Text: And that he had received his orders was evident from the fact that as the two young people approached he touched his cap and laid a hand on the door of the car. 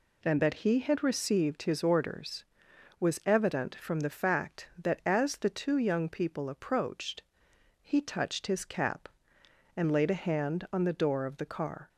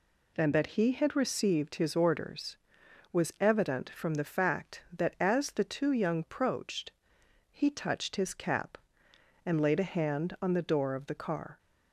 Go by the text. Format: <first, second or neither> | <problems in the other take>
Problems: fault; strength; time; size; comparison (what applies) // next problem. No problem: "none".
first | skips "people"; at 6.2 s // pauses between "approached" and "he"; noticeable; at 6.9 s; 0.58 s long; noticeable in the first